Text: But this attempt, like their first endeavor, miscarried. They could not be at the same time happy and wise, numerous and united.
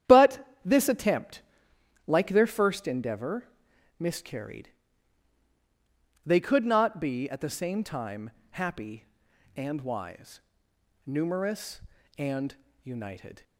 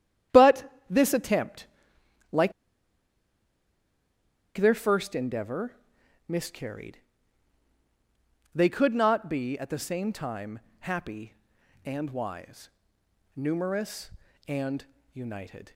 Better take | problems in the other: first | starts louder than the rest; strong; until 1.5 s; 10.5 dB; strong in the first // pauses between "But" and "this"; slight; at 0.7 s; 0.16 s long; slight in the first // pauses between "like" and "their"; strong; at 2.5 s; 2.0 s long // pauses between "time" and "happy"; slight; at 10.5 s; 0.22 s long; slight in the first // pauses between "and" and "united"; slight; at 14.8 s; 0.28 s long; slight in the first

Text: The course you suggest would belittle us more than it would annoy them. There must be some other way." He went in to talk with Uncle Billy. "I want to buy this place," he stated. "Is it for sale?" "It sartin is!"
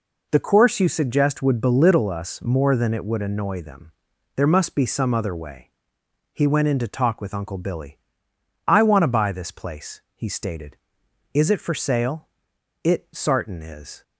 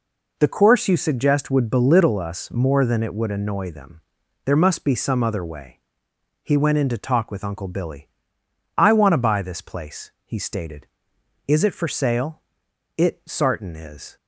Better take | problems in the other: neither | none

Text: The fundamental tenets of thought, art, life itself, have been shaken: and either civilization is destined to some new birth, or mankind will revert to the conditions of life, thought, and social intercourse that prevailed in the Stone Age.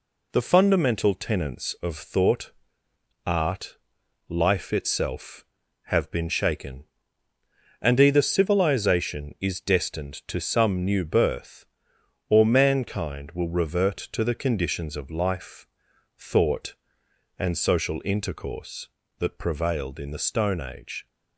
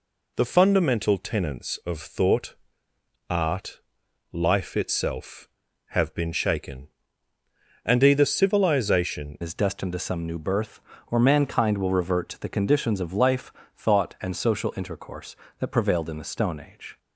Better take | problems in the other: first | changes voice at "is"; from 9.4 s on; 7.5 s long

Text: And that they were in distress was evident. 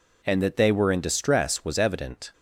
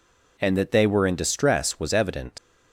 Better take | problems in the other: first | leaves "evident" unfinished; at 2.3 s; 90 ms

